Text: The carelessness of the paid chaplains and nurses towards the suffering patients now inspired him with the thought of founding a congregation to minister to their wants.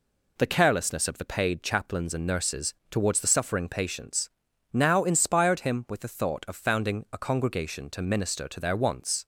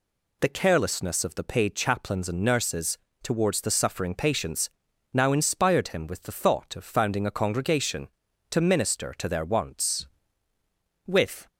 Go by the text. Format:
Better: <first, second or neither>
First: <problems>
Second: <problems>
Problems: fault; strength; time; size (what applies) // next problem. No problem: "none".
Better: first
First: pauses between "nurses" and "towards"; slight; at 2.7 s; 0.16 s long // pauses between "patients" and "now"; noticeable; at 4.2 s; 0.46 s long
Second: pauses between "nurses" and "towards"; slight; at 2.9 s; 0.26 s long // pauses between "patients" and "now"; at 4.6 s; 0.44 s long // goes on to say "With"; slight; from 11.0 s on; 0.44 s long